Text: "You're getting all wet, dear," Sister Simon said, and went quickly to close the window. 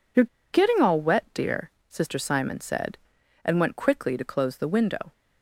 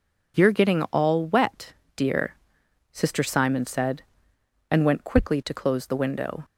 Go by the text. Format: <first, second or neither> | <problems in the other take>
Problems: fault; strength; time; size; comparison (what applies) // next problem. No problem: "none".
second | pauses between "You're" and "getting"; slight; at 0.2 s; 0.27 s long